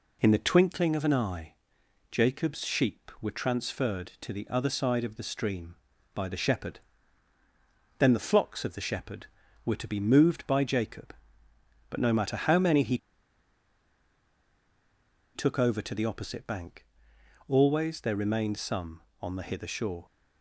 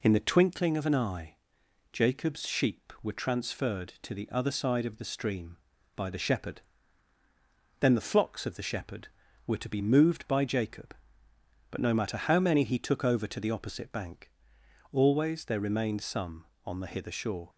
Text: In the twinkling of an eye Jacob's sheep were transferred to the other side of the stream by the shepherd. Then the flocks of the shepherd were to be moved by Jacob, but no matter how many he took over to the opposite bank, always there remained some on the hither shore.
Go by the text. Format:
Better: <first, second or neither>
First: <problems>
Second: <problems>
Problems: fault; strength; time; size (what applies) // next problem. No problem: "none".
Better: second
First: pauses between "eye" and "Jacob's"; noticeable; at 1.5 s; 0.58 s long // pauses between "he" and "took"; strong; at 12.9 s; 2.3 s long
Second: pauses between "eye" and "Jacob's"; noticeable; at 1.3 s; 0.58 s long